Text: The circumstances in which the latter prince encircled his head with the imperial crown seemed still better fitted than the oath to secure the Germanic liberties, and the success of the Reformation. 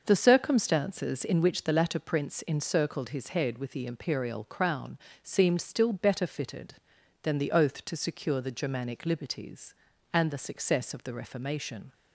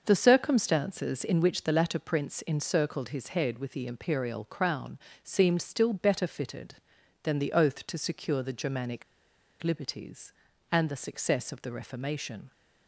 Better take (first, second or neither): first